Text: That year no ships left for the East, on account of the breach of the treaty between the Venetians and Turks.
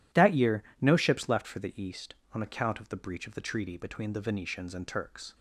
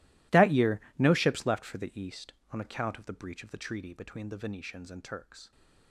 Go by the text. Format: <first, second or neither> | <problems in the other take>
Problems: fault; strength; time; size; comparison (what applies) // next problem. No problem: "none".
first | gets quieter; strong; throughout; 20 dB // pauses between "year" and "no"; slight; at 0.7 s; 0.18 s long; slight in the first